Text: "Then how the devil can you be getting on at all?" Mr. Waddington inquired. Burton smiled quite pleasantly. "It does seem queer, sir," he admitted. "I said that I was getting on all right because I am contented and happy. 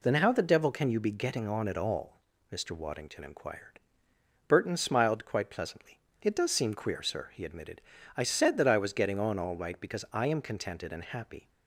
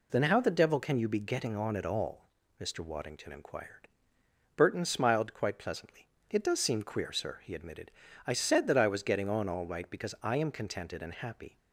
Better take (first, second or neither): neither